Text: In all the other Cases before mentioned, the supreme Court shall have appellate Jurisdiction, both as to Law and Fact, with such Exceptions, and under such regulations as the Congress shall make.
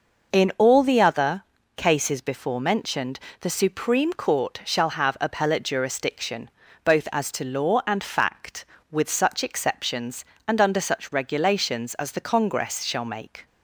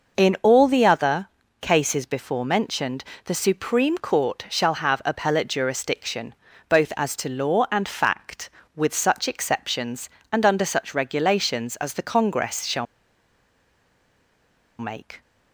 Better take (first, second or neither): first